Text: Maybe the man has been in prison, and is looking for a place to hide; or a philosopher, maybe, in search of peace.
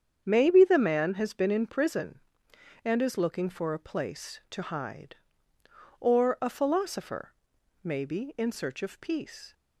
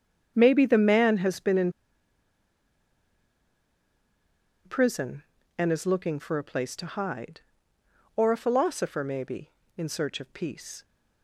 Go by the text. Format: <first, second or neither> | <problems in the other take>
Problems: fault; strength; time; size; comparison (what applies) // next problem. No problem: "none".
first | starts louder than the rest; strong; until 1.3 s; 8 dB; strong in the first // pauses between "in" and "prison"; strong; at 1.7 s; 2.9 s long